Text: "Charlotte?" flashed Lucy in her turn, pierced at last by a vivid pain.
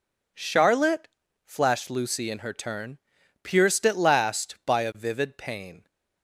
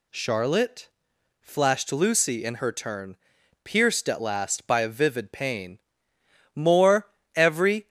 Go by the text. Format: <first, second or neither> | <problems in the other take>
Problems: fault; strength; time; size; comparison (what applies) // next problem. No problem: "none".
first | goes on to say "More every"; from 6.5 s on; 1.3 s long